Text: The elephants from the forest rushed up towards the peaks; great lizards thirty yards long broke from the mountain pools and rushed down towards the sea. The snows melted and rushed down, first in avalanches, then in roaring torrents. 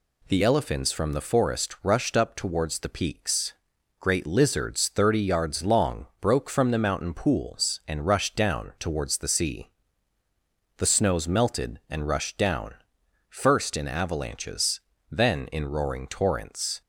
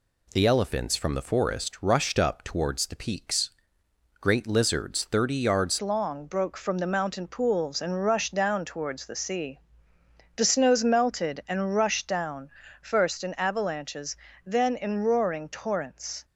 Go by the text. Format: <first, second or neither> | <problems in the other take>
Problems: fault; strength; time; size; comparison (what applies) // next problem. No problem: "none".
first | changes voice at "long"; from 5.8 s on; 10.4 s long